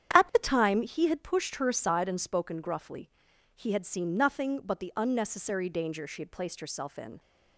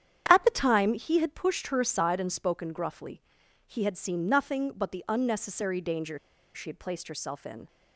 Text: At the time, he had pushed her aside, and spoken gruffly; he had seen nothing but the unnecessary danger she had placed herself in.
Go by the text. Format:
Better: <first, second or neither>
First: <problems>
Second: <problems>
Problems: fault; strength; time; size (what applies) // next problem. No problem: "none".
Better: first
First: starts louder than the rest; strong; until 1.2 s; 9.5 dB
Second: starts louder than the rest; strong; until 1.2 s; 9.5 dB // pauses between "danger" and "she"; at 6.1 s; 0.36 s long